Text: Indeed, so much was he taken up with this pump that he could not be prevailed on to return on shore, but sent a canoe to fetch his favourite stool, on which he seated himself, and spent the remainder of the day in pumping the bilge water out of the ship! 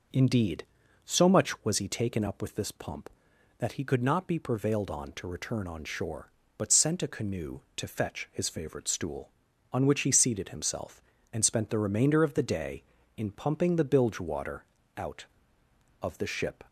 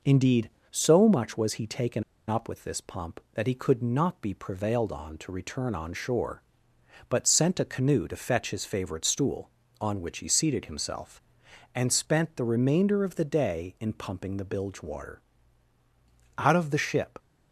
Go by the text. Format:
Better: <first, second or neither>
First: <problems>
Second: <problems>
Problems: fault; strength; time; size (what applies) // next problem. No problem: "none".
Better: first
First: pauses between "water" and "out"; slight; at 14.6 s; 0.34 s long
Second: pauses between "taken" and "up"; slight; at 2.0 s; 0.24 s long // pauses between "water" and "out"; at 15.2 s; 1.1 s long